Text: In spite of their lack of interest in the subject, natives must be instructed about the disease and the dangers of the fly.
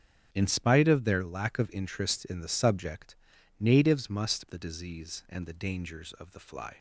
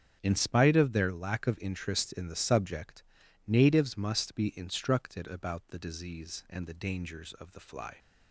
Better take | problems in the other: second | starts louder than the rest; strong; until 1.3 s; 8.5 dB; strong in the second // skips "be instructed about"; at 4.4 s

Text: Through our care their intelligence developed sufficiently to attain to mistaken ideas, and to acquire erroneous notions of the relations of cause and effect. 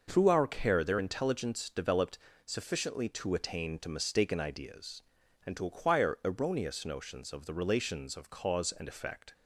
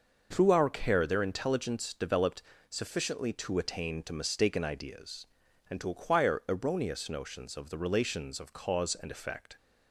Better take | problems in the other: neither | pauses between "developed" and "sufficiently"; slight; the same in both

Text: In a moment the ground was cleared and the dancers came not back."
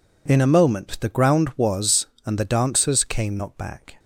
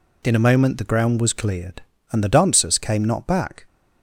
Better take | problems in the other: second | skips "cleared"; at 2.1 s

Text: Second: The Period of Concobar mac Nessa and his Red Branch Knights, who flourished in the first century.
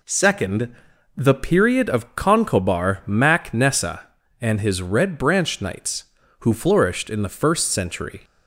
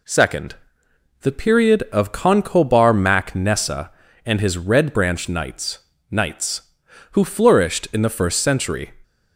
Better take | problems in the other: first | says "Knights" twice; at 6.1 s

